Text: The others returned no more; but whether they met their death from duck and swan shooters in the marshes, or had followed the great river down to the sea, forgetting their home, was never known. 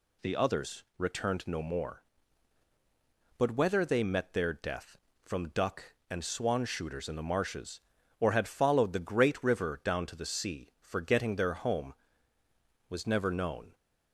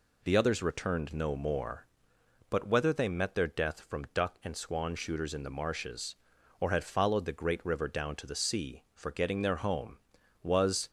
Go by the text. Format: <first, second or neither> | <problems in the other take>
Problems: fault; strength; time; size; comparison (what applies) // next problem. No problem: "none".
first | stops before "never known"; at 10.8 s